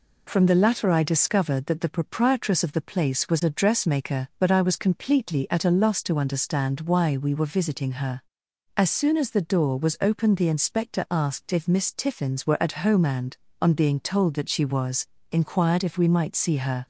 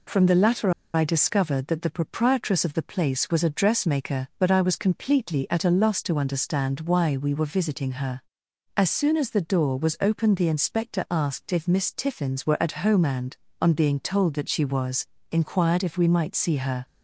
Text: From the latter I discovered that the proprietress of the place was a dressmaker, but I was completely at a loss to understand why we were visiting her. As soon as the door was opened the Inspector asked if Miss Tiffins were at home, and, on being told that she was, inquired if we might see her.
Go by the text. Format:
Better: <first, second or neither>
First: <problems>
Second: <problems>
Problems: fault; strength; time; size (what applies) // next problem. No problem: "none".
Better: first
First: none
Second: pauses between "latter" and "I"; slight; at 0.6 s; 0.24 s long